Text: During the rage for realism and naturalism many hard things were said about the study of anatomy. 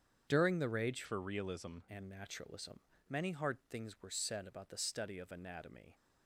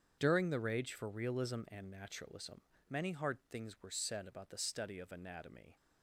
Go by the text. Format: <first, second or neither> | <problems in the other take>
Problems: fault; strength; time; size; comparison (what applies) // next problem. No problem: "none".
second | starts louder than the rest; strong; until 1.3 s; 8 dB; strong in the second // changes voice from "for" to "realism"; from 1.0 to 1.7 s; 0.7 s long // pauses between "naturalism" and "many"; slight; at 2.8 s; 0.28 s long; slight in the second